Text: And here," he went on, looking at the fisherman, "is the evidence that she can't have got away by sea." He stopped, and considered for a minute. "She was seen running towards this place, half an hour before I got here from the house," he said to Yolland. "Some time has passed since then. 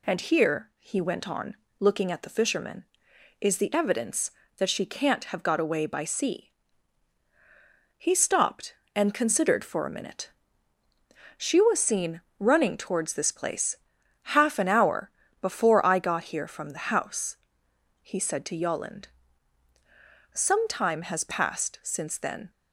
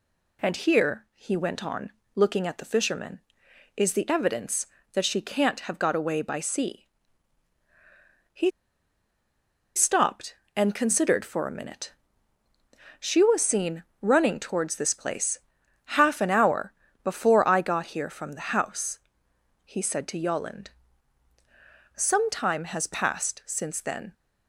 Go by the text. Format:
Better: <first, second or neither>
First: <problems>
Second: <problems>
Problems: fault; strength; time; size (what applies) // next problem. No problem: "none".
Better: first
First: pauses between "seen" and "running"; slight; at 12.2 s; 0.18 s long // pauses between "hour" and "before"; slight; at 15.1 s; 0.30 s long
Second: pauses between "He" and "stopped"; strong; at 8.4 s; 1.2 s long // pauses between "seen" and "running"; slight; at 13.8 s; 0.18 s long // pauses between "hour" and "before"; slight; at 16.7 s; 0.30 s long